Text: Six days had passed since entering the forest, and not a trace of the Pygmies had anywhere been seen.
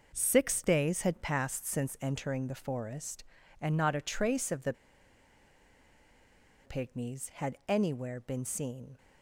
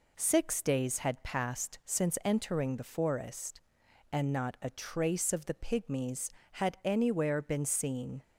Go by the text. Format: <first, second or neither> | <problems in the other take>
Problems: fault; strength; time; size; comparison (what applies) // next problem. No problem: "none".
second | pauses between "the" and "Pygmies"; strong; at 4.7 s; 1.9 s long